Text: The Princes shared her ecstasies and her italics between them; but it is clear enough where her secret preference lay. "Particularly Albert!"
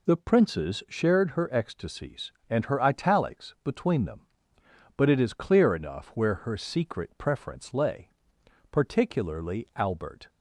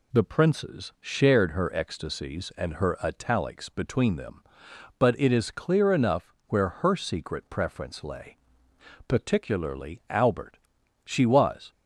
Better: first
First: none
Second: pauses between "enough" and "where"; slight; at 6.3 s; 0.16 s long // goes on to say "She was"; noticeable; from 11.0 s on; 0.66 s long

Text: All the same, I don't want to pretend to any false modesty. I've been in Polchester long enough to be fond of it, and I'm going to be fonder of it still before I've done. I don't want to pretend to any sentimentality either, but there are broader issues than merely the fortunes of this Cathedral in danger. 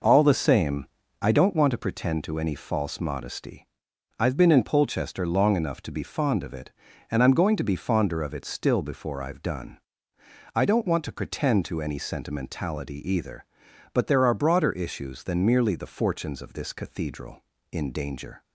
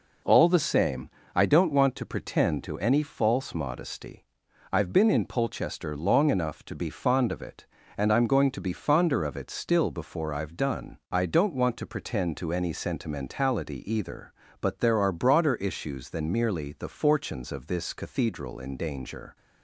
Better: neither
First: none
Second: none

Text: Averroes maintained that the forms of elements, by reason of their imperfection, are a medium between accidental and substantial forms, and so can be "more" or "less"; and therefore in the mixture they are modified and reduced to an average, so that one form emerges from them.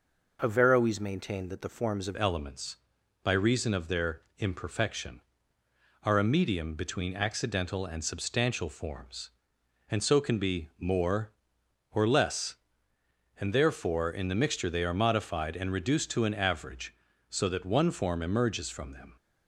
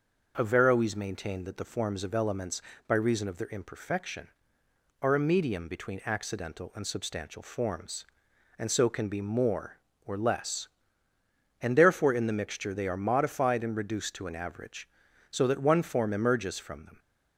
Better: second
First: changes voice at "elements"; from 2.1 s on; 17.0 s long // pauses between "their" and "imperfection"; slight; at 4.2 s; 0.16 s long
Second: none

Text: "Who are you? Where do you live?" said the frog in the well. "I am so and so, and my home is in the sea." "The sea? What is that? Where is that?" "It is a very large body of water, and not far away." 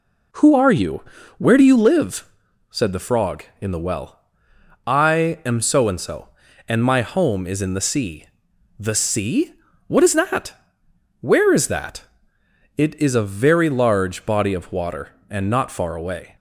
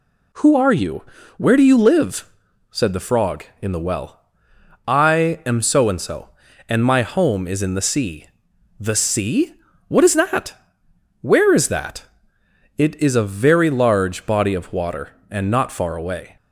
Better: second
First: starts louder than the rest; until 1.8 s; 3.5 dB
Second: none

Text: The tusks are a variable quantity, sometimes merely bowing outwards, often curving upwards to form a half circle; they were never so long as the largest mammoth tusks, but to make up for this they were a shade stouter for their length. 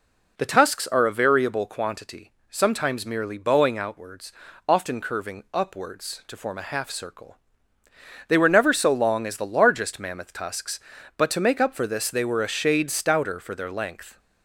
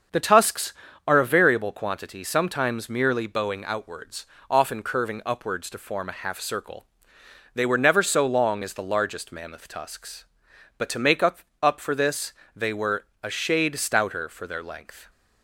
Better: first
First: none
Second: starts louder than the rest; until 1.4 s; 7 dB // says "up" twice; at 11.6 s // pauses between "this" and "they"; slight; at 12.3 s; 0.24 s long // pauses between "were" and "a"; slight; at 13.0 s; 0.18 s long

